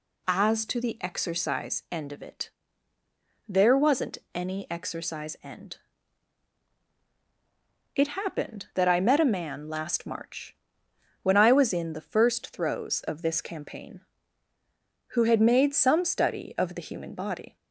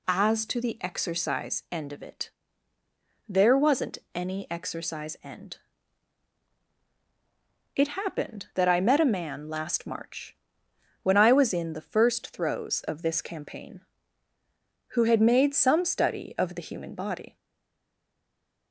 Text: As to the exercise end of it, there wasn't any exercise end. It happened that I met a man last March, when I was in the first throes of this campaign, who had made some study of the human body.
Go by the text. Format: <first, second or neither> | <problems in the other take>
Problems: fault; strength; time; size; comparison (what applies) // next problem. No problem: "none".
first | pauses between "wasn't" and "any"; slight; at 3.9 s; 0.16 s long; slight in the first // stays silent after the last word; noticeable; from 17.3 s on; 1.4 s long